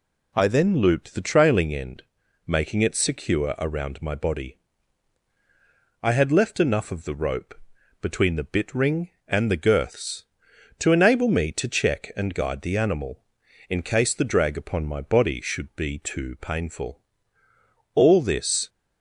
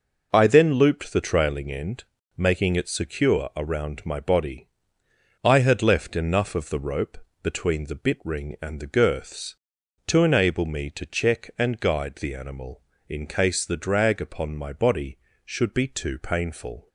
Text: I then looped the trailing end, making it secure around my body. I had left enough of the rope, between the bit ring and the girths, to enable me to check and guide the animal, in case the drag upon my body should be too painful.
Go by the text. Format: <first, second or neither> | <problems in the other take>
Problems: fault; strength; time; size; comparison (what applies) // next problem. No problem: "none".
second | goes on to say "All this"; noticeable; from 17.9 s on; 0.74 s long